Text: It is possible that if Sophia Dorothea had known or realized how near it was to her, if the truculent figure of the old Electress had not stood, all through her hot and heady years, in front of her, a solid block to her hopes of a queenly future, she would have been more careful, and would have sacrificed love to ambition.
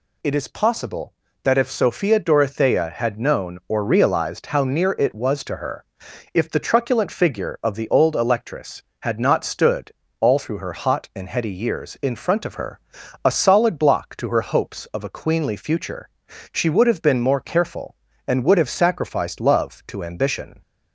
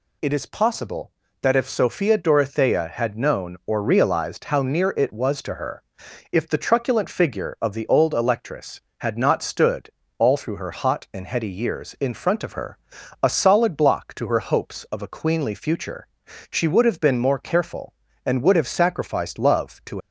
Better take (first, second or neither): first